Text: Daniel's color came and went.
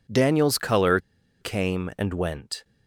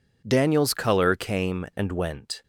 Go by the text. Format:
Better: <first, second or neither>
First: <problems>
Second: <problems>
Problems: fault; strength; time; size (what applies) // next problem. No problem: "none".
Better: second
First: pauses between "color" and "came"; at 0.9 s; 0.43 s long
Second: none